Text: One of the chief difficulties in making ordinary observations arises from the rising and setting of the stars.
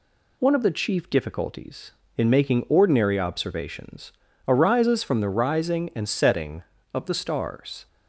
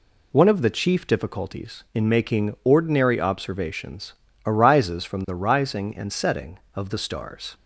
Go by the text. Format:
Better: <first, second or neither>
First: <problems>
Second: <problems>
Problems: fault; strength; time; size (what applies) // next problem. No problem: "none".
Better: neither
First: pauses between "observations" and "arises"; slight; at 4.1 s; 0.34 s long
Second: pauses between "observations" and "arises"; slight; at 4.1 s; 0.32 s long